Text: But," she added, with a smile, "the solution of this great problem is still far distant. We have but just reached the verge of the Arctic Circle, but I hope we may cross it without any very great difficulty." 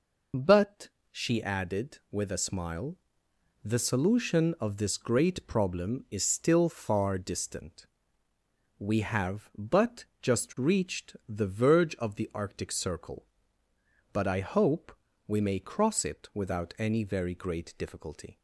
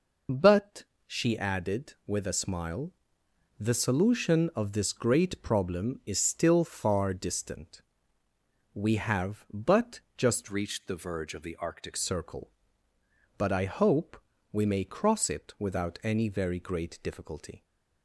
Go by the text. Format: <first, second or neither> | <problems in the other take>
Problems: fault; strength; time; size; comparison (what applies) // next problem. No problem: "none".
first | pauses between "but" and "just"; slight; at 9.9 s; 0.18 s long; slight in the first // changes voice from "reached" to "Arctic"; from 10.4 to 11.9 s; 1.5 s long // pauses between "hope" and "we"; slight; at 14.2 s; 0.30 s long; slight in the first